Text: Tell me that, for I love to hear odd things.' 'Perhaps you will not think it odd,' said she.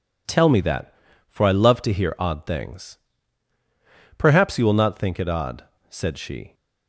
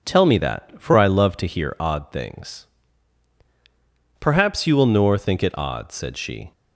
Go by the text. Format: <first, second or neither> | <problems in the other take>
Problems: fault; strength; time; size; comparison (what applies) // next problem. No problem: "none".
first | says "nor" for "not"; at 4.8 s